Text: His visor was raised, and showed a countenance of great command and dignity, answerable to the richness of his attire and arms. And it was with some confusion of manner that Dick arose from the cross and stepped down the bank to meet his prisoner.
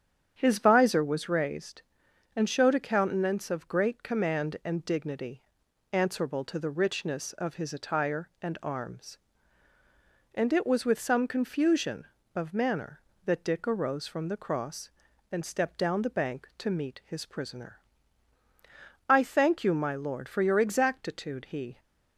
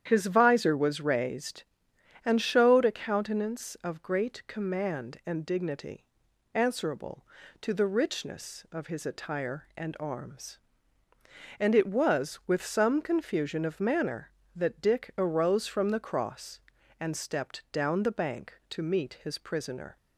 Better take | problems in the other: second | starts louder than the rest; strong; until 1.3 s; 8.5 dB; strong in the second // goes on to say "I thank you my lord for your exactitude he"; strong; from 19.0 s on; 2.7 s long

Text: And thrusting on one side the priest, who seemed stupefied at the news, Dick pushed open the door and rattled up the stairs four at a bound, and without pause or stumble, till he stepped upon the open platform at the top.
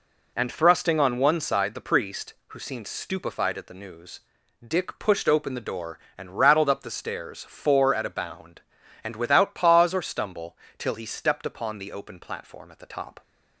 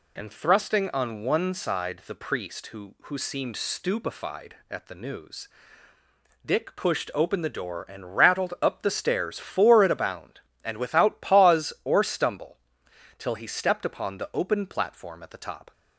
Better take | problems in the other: first | says "who" twice; at 3.0 s

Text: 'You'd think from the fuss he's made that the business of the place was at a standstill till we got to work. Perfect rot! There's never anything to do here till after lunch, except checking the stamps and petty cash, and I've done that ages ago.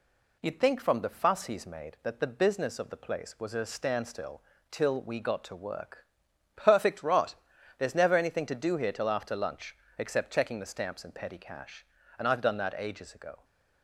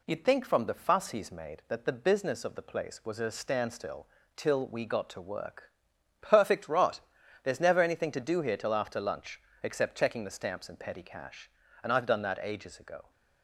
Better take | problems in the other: neither | pauses between "standstill" and "till"; slight; the same in both

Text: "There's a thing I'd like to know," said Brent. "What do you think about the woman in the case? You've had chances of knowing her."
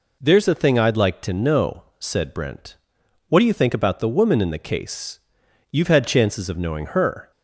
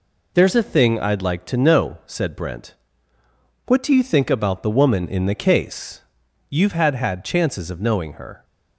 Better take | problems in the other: first | says "had" twice; at 6.9 s

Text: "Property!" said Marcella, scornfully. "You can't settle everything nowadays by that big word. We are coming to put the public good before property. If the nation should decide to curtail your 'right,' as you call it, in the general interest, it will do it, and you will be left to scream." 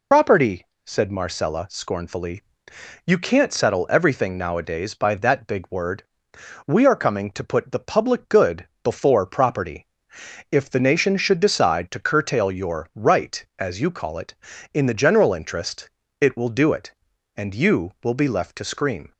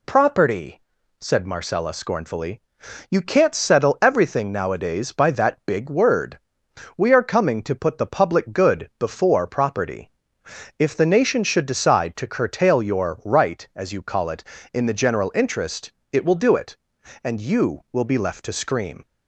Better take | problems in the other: second | loses the start of "Property"; at 0.1 s; 90 ms // pauses between "good" and "before"; slight; at 8.6 s; 0.16 s long

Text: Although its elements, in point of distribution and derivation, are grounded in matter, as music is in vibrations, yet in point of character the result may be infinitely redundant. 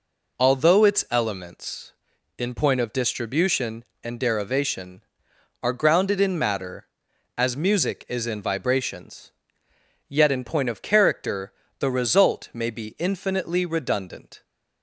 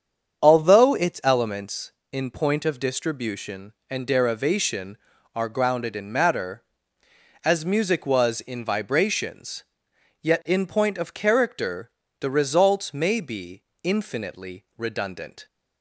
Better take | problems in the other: first | starts louder than the rest; strong; until 1.4 s; 7.5 dB // says "was" for "is"; at 8.0 s // pauses between "character" and "the"; slight; at 11.9 s; 0.28 s long; slight in the first // pauses between "be" and "infinitely"; slight; at 13.6 s; 0.20 s long

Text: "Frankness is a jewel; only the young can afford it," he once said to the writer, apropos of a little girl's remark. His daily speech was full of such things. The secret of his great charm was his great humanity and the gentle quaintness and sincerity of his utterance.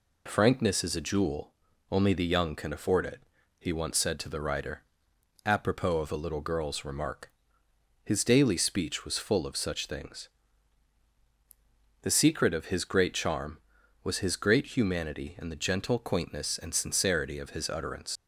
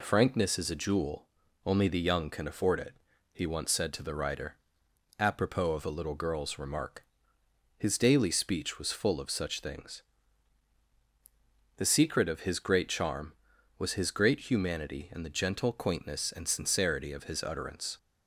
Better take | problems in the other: second | leaves "utterance" unfinished; at 18.1 s; 80 ms

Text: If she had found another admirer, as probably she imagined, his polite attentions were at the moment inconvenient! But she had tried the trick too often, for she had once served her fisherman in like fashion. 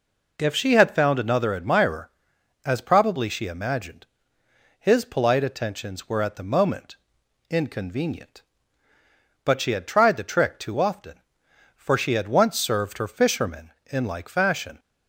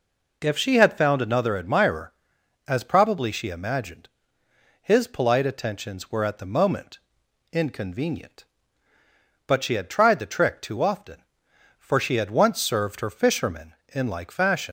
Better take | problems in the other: first | pauses between "moment" and "inconvenient"; noticeable; at 6.9 s; 0.52 s long; noticeable in the first // leaves "fashion" unfinished; at 14.6 s; 100 ms

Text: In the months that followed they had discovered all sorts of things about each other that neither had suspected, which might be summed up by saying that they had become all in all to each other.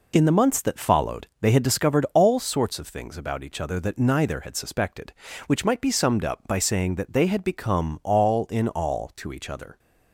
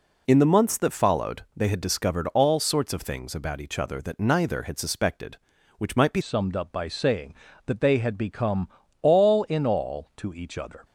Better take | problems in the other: first | changes voice at "summed"; from 6.2 s on; 4.6 s long // pauses between "become" and "all"; slight; at 8.6 s; 0.32 s long

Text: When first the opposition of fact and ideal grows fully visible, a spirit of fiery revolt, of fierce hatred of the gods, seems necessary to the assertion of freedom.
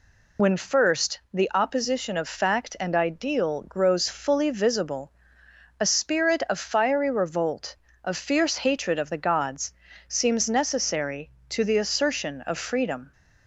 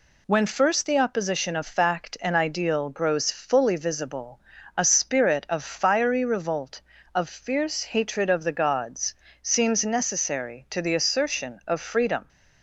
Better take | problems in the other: second | loses the start of "When"; at 0.3 s; 60 ms

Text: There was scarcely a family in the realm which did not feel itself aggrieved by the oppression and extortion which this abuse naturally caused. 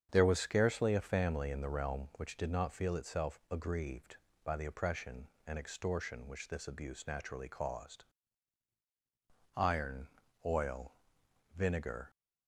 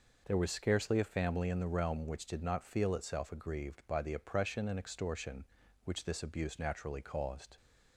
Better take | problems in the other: second | starts louder than the rest; strong; until 1.1 s; 7.5 dB // goes on to say "Iron oil vinegar"; strong; from 9.5 s on; 2.5 s long

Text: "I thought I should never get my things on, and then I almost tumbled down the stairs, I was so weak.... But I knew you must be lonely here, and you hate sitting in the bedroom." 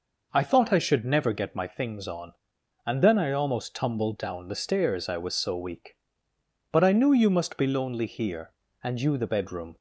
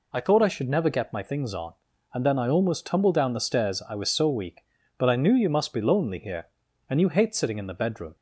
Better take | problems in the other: second | skips "hate sitting in"; at 9.1 s

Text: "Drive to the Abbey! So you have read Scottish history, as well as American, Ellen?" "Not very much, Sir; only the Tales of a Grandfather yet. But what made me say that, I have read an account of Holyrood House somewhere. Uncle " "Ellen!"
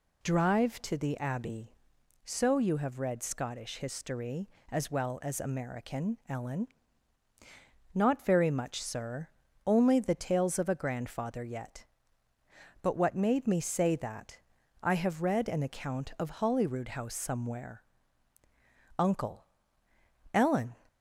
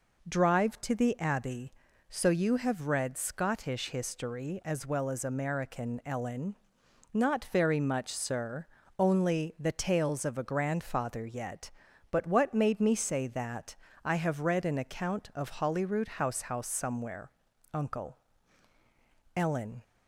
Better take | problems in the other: first | says "House" twice; at 16.4 s

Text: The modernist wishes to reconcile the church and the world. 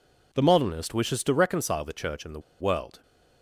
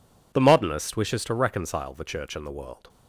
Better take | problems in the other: second | pauses between "the" and "world"; slight; at 2.3 s; 0.20 s long

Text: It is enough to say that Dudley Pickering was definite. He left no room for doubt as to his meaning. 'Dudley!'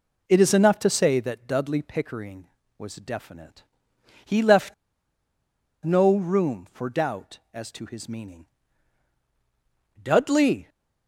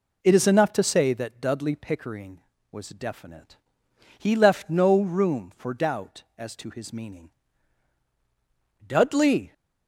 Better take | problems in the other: second | pauses between "left" and "no"; at 4.7 s; 1.1 s long

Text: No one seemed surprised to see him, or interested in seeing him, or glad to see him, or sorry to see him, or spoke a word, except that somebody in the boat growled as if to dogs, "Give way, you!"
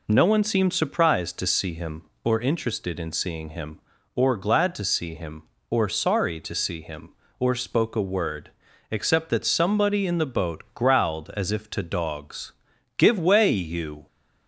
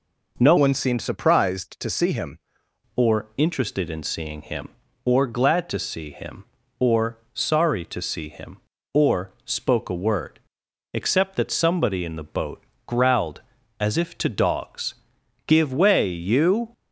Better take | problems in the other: first | changes voice from "one" to "him"; from 0.5 to 2.3 s; 1.8 s long // pauses between "or" and "sorry"; slight; at 7.1 s; 0.16 s long // pauses between "boat" and "growled"; slight; at 12.6 s; 0.24 s long

